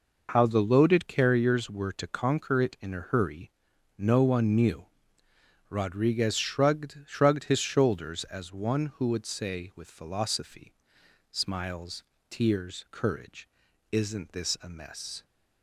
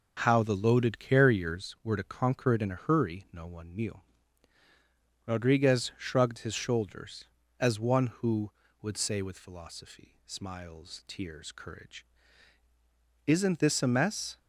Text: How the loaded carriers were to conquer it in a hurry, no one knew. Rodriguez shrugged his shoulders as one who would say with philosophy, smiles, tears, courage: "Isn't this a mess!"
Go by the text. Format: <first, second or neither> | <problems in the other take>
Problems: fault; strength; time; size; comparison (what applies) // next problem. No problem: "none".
second | says "shrugged" twice; at 7.0 s